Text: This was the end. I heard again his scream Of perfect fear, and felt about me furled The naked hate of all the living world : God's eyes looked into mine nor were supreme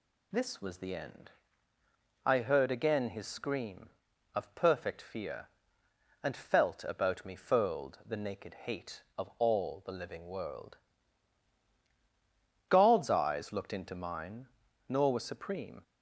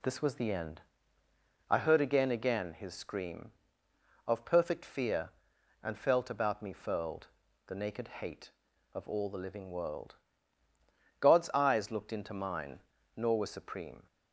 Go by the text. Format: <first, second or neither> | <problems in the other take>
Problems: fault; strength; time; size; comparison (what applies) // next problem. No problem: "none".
first | says "again" twice; at 2.3 s // pauses between "furled" and "The"; at 7.2 s; 0.40 s long // pauses between "mine" and "nor"; slight; at 12.8 s; 0.34 s long; also in the first